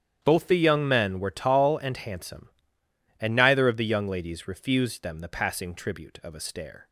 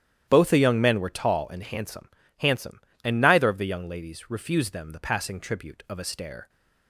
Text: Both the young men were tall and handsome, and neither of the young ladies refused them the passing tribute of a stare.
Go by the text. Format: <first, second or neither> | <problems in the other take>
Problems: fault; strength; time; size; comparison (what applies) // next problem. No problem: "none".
first | starts louder than the rest; strong; until 1.2 s; 11 dB; strong in the first // says "handsome" twice; at 2.3 s